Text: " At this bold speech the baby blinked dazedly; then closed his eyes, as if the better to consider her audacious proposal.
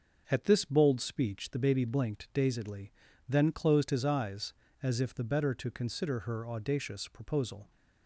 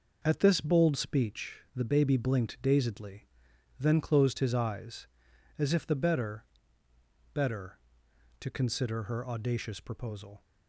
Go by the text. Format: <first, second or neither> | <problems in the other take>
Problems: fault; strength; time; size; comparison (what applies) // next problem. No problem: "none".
first | says "better" twice; at 7.3 s